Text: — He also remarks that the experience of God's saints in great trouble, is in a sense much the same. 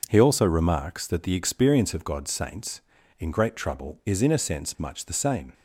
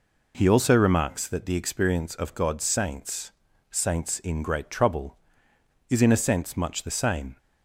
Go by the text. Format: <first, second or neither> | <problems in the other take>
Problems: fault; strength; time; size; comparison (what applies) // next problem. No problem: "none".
first | says "saints" twice; at 3.6 s